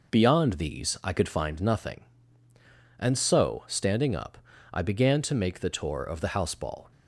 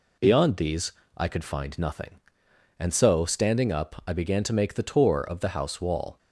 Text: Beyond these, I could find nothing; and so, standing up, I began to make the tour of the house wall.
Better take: second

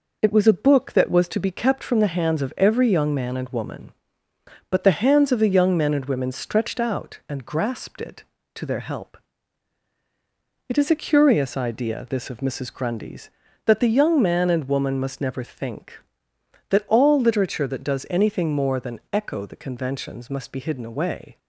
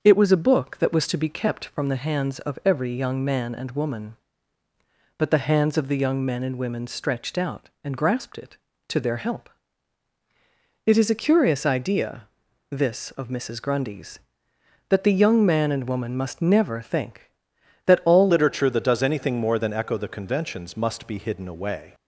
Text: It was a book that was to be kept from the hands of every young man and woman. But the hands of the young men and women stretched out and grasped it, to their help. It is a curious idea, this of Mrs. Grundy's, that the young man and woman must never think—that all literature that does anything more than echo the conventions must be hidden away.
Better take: first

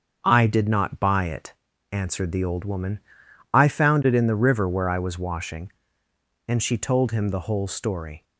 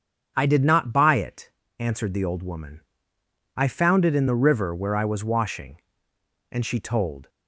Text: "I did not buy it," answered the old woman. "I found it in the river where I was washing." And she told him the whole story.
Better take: first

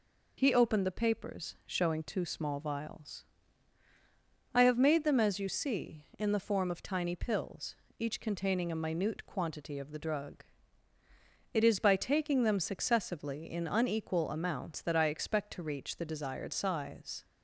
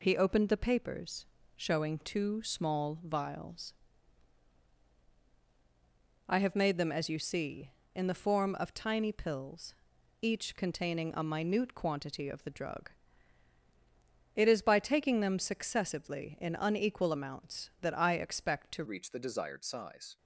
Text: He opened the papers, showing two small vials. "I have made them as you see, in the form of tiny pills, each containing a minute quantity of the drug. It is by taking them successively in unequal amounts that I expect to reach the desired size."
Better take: first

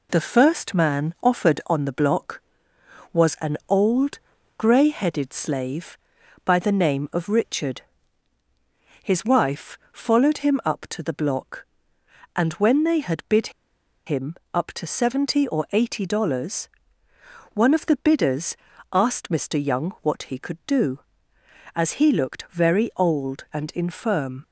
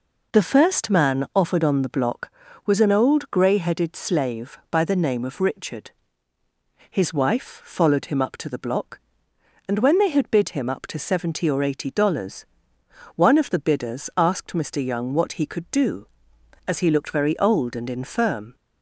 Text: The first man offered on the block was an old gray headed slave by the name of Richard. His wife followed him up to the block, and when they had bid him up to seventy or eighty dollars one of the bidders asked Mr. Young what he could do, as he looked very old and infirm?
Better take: second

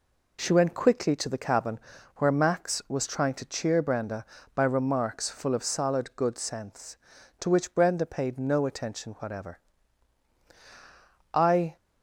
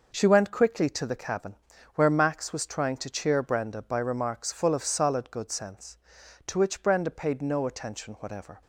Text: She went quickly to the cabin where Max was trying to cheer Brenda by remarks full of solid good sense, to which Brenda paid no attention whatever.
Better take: second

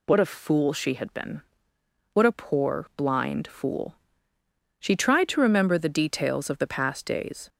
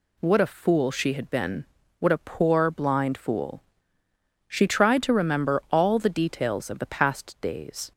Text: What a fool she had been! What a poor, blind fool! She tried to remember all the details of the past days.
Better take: second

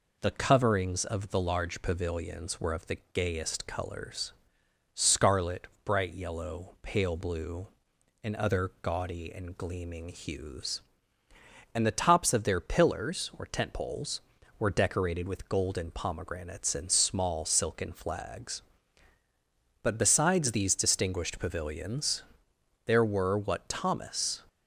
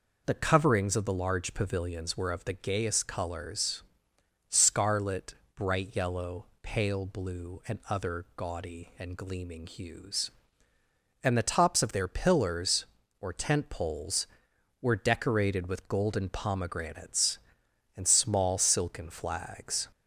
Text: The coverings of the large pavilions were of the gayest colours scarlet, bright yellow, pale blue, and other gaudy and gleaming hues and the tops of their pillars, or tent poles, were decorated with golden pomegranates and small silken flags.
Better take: second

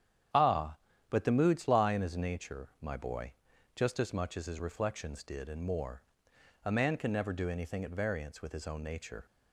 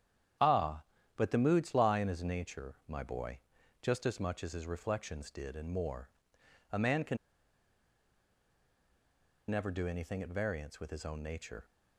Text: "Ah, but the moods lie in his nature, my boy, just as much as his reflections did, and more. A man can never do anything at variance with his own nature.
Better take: first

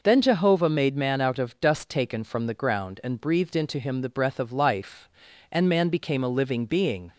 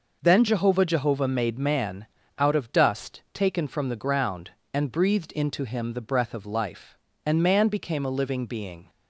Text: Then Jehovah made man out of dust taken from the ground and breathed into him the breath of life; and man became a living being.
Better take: first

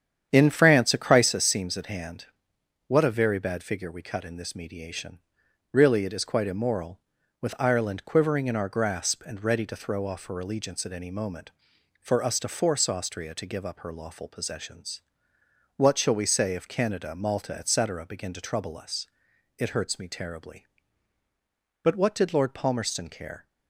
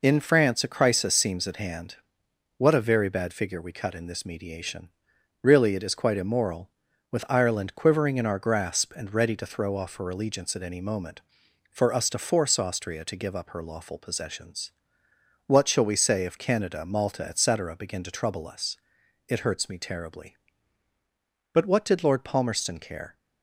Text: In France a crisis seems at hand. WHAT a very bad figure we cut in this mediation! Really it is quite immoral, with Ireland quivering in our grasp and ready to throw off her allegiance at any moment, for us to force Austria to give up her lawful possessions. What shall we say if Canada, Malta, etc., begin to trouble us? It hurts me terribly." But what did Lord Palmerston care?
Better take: second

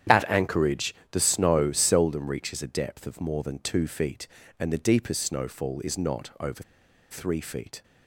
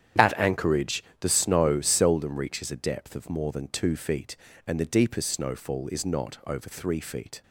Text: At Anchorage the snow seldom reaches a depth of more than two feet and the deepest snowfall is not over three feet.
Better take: second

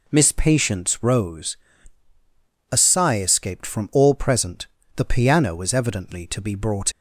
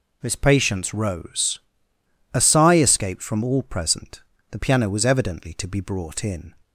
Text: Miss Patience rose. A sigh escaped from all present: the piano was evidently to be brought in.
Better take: second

